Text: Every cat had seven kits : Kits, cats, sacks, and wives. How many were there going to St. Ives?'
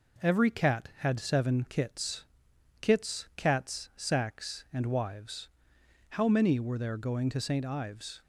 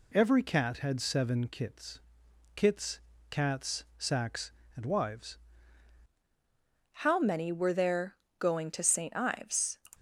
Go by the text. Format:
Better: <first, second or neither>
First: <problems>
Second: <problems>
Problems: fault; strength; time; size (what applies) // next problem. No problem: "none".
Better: first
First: none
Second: changes voice at "How"; from 6.9 s on; 2.8 s long // pauses between "there" and "going"; slight; at 8.1 s; 0.22 s long